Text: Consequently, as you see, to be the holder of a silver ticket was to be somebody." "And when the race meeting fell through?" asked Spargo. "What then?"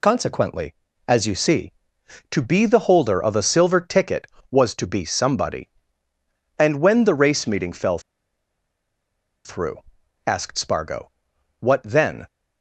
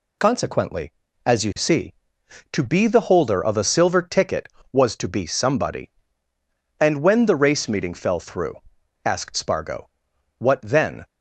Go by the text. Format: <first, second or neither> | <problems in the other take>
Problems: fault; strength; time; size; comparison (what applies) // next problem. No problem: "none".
second | pauses between "fell" and "through"; strong; at 7.9 s; 1.4 s long